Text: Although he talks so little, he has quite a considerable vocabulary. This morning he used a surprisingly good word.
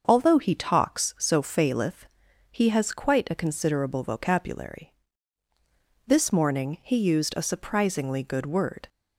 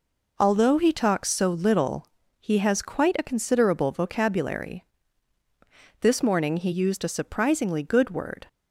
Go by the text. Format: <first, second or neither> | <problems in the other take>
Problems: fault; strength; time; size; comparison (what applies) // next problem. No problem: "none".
second | starts louder than the rest; until 1.0 s; 6.5 dB // says "faileth" for "little"; at 1.4 s